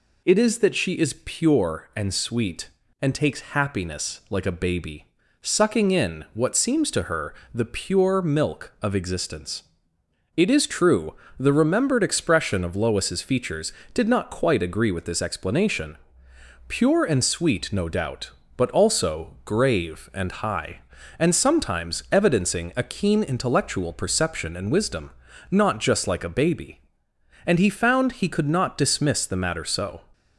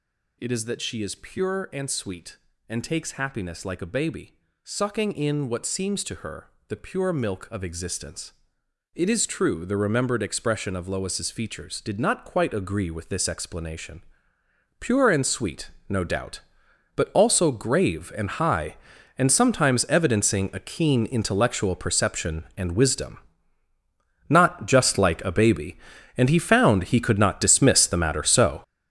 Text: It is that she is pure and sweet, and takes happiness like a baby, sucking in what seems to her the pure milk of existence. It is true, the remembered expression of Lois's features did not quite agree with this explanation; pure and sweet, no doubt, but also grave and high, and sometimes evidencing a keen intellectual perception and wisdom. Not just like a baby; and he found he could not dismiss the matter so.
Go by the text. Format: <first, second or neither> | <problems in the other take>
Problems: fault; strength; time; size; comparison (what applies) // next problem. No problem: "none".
first | gets louder; strong; throughout; 10.5 dB // pauses between "her" and "the"; slight; at 6.4 s; 0.20 s long; slight in the first